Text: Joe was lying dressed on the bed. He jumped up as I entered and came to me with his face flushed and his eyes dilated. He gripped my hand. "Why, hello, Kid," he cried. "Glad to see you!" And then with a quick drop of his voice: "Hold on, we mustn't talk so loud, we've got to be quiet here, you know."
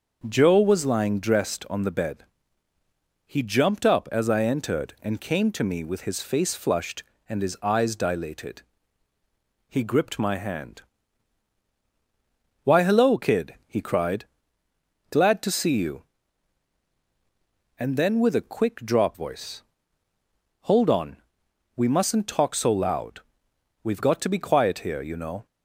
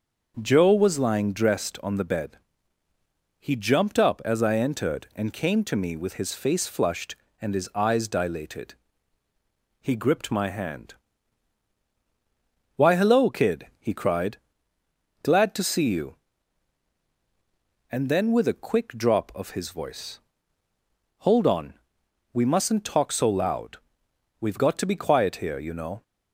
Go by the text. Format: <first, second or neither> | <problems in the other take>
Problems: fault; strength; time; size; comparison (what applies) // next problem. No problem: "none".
second | skips "of his"; at 19.1 s